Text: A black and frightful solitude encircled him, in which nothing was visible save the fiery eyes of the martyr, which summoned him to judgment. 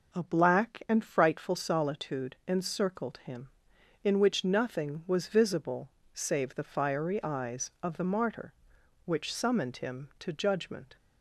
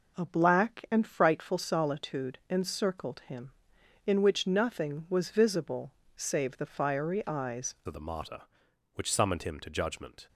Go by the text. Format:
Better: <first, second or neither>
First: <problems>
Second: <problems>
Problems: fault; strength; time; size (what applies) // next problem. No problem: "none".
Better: first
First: pauses between "visible" and "save"; slight; at 5.8 s; 0.24 s long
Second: pauses between "visible" and "save"; slight; at 5.9 s; 0.24 s long // changes voice at "of"; from 7.8 s on; 2.4 s long